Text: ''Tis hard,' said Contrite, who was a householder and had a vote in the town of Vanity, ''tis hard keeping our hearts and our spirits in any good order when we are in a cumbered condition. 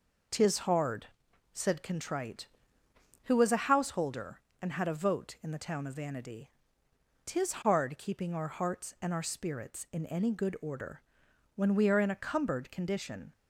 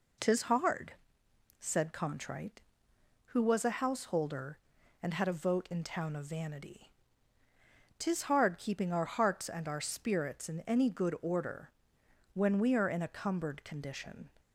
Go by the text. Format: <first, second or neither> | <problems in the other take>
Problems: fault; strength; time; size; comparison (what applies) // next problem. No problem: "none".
first | skips "the"; at 5.8 s // pauses between "order" and "when"; noticeable; at 11.6 s; 0.64 s long; noticeable in the first